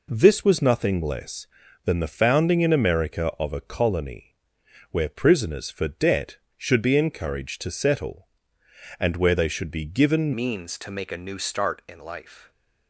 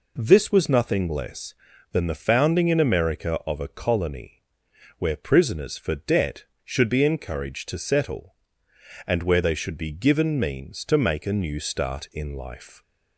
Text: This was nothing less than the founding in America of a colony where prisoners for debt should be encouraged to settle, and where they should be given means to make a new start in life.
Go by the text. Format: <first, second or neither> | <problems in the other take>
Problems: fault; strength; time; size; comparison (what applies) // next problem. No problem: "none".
second | pauses between "colony" and "where"; noticeable; at 4.3 s; 0.54 s long; noticeable in the second // changes voice at "means"; from 10.3 s on; 2.2 s long // stays silent after the last word; slight; from 12.3 s on; 0.5 s long